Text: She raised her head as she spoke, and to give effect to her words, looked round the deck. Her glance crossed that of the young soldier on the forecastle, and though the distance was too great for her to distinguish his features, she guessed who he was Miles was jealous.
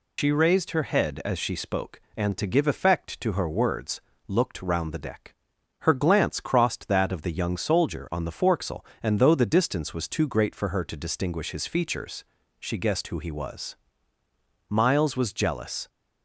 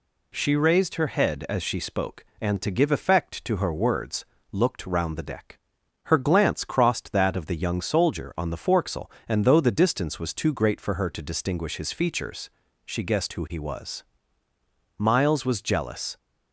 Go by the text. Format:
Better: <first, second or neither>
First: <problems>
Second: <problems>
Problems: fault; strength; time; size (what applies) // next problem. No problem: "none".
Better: second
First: loses the start of "She"; at 0.1 s; 95 ms // pauses between "was" and "Miles"; noticeable; at 13.7 s; 0.92 s long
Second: pauses between "was" and "Miles"; noticeable; at 14.0 s; 0.94 s long